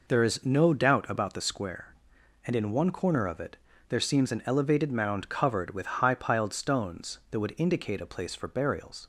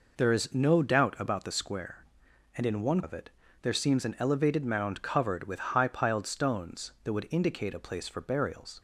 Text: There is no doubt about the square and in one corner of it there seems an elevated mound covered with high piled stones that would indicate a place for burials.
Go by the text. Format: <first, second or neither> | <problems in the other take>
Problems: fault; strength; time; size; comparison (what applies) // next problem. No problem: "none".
first | skips "corner"; at 3.0 s // pauses between "it" and "there"; slight; at 3.3 s; 0.32 s long; slight in the first